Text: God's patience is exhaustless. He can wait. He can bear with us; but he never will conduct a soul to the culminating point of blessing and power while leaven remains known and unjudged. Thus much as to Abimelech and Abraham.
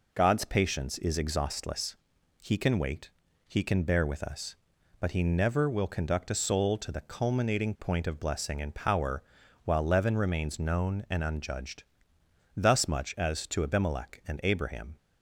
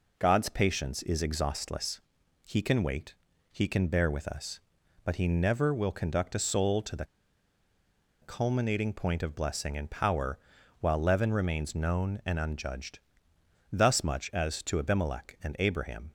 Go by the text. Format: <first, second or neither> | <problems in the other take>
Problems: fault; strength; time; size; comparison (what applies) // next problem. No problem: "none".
first | pauses between "the" and "culminating"; at 7.0 s; 1.1 s long // pauses between "power" and "while"; at 10.3 s; 0.42 s long; also in the first